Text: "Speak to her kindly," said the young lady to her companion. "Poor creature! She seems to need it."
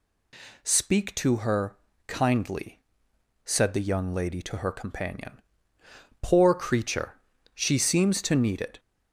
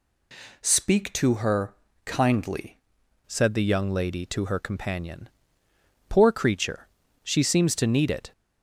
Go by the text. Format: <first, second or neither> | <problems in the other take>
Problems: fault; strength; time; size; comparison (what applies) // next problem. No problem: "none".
first | pauses between "her" and "kindly"; slight; at 1.7 s; 0.32 s long; slight in the first // changes voice at "said"; from 3.2 s on; 5.1 s long